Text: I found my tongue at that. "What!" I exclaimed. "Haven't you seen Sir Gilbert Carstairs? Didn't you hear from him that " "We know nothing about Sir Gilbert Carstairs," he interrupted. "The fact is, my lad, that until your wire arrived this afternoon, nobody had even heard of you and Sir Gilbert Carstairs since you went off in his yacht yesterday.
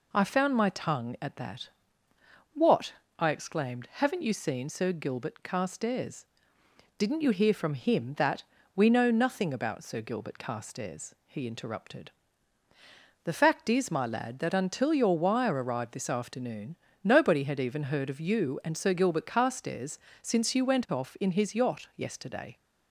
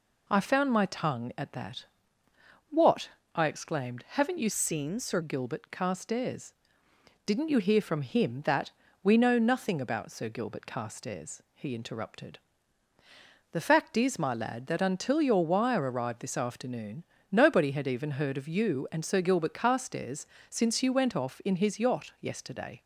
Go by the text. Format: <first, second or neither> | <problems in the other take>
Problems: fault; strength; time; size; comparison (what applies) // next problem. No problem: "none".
first | changes voice from "seen" to "Sir"; from 4.5 to 5.1 s; 0.6 s long // pauses between "Carstairs" and "since"; slight; at 20.2 s; 0.24 s long; slight in the first